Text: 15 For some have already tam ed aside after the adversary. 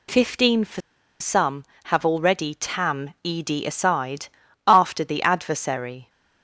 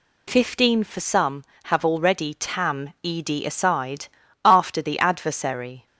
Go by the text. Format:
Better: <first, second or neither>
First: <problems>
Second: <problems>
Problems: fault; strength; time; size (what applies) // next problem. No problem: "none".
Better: second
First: pauses between "For" and "some"; at 0.8 s; 0.40 s long // pauses between "aside" and "after"; at 4.2 s; 0.38 s long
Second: pauses between "aside" and "after"; slight; at 4.0 s; 0.36 s long